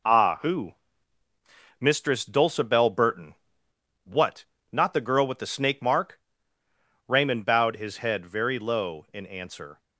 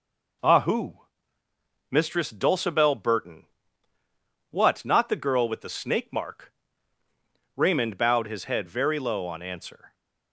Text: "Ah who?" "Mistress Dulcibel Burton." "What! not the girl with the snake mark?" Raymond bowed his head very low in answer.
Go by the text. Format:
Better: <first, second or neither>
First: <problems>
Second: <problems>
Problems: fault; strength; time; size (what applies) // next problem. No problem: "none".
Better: first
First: none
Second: says "on" for "in"; at 9.2 s